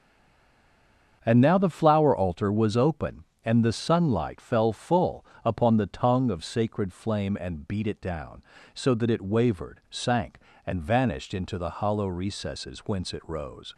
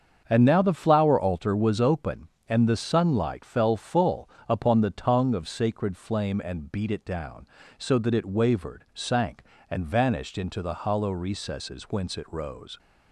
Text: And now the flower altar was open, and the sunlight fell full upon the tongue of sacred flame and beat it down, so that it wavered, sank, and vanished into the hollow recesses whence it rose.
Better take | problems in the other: second | stays silent before the first word; noticeable; until 1.2 s; 1.2 s long // starts louder than the rest; strong; until 2.2 s; 7 dB; strong in the second // pauses between "full" and "upon"; slight; at 5.2 s; 0.18 s long; slight in the second

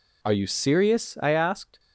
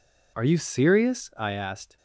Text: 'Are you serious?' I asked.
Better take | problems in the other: neither | none

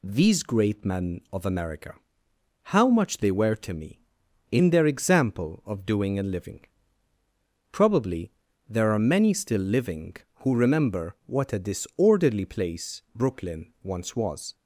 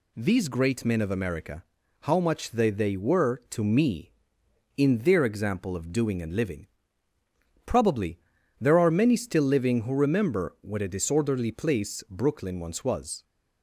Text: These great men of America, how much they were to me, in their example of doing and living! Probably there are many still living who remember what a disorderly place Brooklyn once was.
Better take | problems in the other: first | says "they" twice; at 2.6 s // pauses between "Probably" and "there"; at 8.1 s; 0.40 s long; also in the first

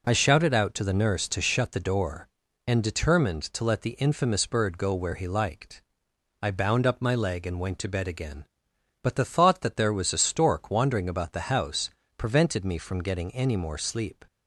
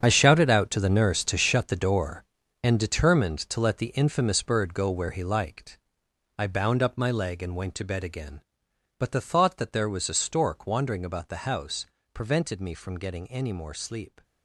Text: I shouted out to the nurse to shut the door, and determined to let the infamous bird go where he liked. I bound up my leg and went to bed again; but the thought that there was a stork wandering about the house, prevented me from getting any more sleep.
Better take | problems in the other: first | gets quieter; strong; throughout; 13 dB

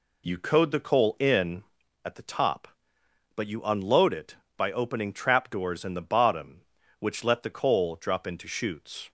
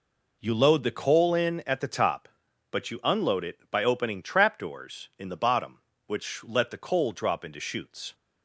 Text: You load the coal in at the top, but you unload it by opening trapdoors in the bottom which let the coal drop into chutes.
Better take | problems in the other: second | says "code" for "load"; at 0.3 s

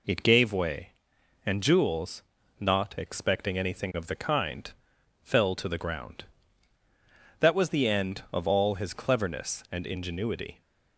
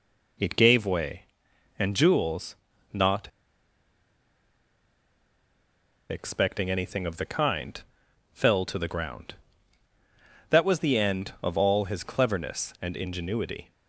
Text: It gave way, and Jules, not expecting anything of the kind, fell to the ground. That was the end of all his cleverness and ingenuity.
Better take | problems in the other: first | pauses between "not" and "expecting"; strong; at 3.2 s; 2.8 s long

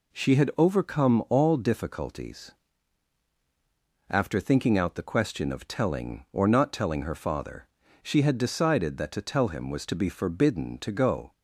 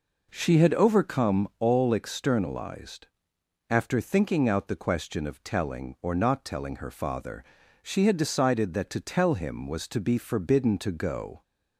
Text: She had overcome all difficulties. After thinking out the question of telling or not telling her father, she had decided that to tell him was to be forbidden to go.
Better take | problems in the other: first | says "externalized" for "difficulties"; at 1.9 s

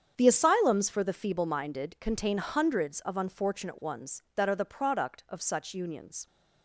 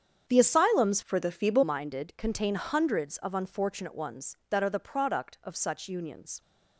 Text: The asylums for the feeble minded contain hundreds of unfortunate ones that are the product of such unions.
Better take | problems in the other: first | starts louder than the rest; strong; until 1.2 s; 8 dB; strong in the first // changes voice from "for" to "feeble"; from 1.0 to 1.6 s; 0.6 s long

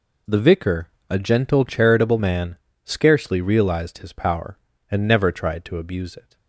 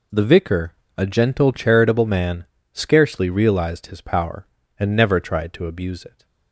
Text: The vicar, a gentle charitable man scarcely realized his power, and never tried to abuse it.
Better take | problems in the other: neither | pauses between "man" and "scarcely"; slight; the same in both

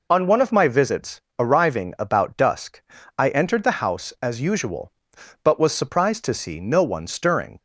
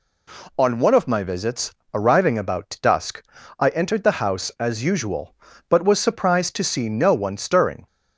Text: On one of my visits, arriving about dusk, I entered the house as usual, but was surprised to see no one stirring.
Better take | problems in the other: neither | none

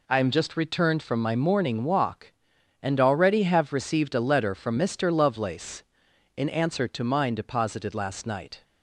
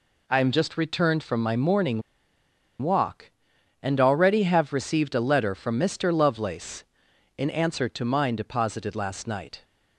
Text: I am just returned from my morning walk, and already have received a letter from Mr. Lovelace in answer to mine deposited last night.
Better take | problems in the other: first | pauses between "morning" and "walk"; noticeable; at 2.0 s; 0.80 s long

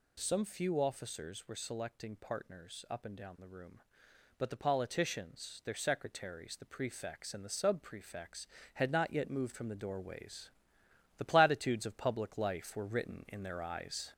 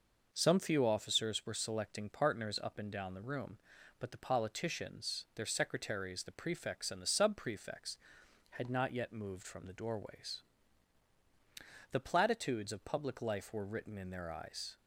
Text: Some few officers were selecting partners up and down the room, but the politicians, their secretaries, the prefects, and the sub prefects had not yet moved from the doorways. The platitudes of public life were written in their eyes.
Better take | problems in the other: second | gets louder; throughout; 4 dB

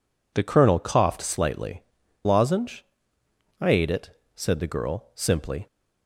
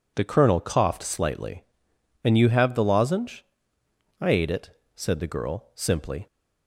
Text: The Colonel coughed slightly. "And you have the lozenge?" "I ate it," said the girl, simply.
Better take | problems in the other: second | skips "And you have the"; at 2.0 s

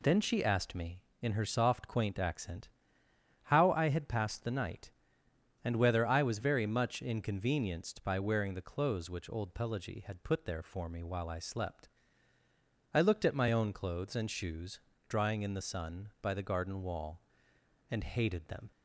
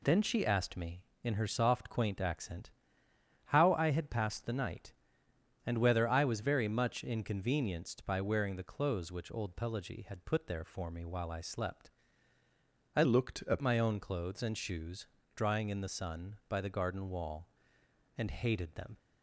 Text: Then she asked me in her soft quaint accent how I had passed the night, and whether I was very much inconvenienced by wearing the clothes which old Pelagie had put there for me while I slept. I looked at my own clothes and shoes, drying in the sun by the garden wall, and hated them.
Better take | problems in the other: first | pauses between "accent" and "how"; noticeable; at 2.7 s; 0.74 s long; noticeable in the first // changes voice from "looked" to "at"; from 13.0 to 13.6 s; 0.6 s long

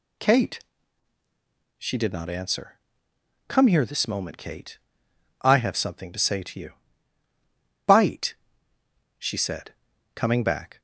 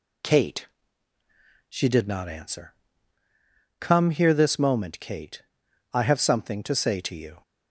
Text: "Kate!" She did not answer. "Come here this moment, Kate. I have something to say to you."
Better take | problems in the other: second | goes on to say "Bite she said coming back"; strong; from 7.8 s on; 2.9 s long

